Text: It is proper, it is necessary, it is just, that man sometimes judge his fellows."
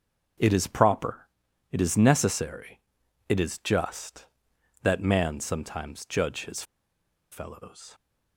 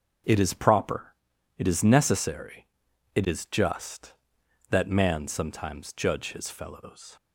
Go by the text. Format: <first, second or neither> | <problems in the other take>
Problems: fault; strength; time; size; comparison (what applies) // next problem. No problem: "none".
second | starts louder than the rest; until 1.8 s; 6.5 dB; also in the second // pauses between "his" and "fellows"; noticeable; at 6.6 s; 0.69 s long